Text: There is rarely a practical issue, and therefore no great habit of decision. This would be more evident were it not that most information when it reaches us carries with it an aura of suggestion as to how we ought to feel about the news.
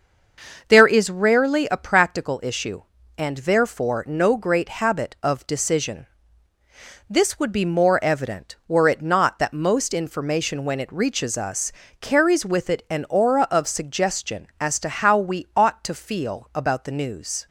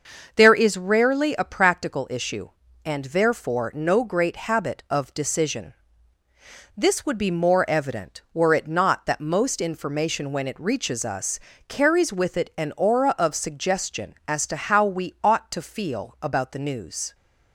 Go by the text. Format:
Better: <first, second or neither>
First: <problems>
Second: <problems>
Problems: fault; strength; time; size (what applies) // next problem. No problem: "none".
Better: neither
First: starts louder than the rest; noticeable; until 1.6 s; 6 dB // pauses between "us" and "carries"; slight; at 11.7 s; 0.30 s long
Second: starts louder than the rest; until 1.3 s; 6 dB // pauses between "us" and "carries"; slight; at 11.3 s; 0.30 s long